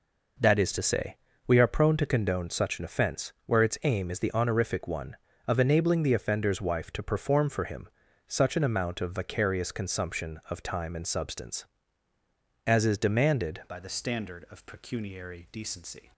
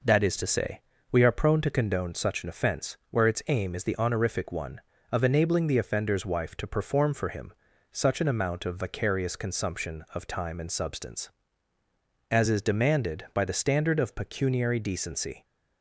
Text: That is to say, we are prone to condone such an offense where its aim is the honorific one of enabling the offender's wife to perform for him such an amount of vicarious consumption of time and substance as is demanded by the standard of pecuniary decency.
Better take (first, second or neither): second